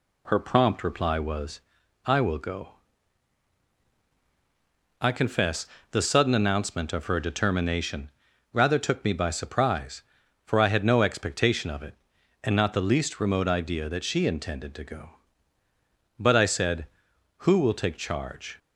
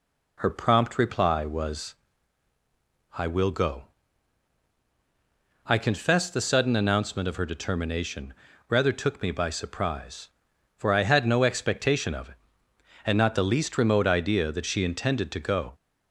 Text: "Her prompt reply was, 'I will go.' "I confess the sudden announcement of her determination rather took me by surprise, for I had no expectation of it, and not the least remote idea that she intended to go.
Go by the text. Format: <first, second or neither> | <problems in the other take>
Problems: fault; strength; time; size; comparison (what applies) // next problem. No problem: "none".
second | pauses between "confess" and "the"; slight; at 5.6 s; 0.24 s long // pauses between "determination" and "rather"; at 8.1 s; 0.42 s long; slight in the second // goes on to say "But I said who will take charge"; strong; from 16.1 s on; 2.4 s long